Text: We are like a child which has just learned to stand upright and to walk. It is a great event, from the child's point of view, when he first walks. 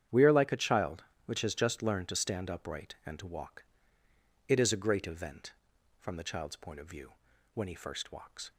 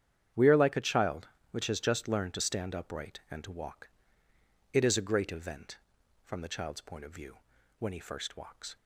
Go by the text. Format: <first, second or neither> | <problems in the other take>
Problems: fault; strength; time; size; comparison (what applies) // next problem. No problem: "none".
neither | starts louder than the rest; strong; the same in both